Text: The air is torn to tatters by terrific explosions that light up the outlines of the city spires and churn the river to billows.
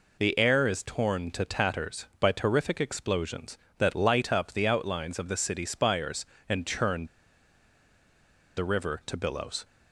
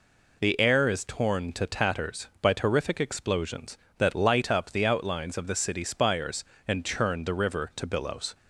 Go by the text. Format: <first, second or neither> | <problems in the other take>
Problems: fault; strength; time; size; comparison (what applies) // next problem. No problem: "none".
second | pauses between "churn" and "the"; strong; at 7.0 s; 1.5 s long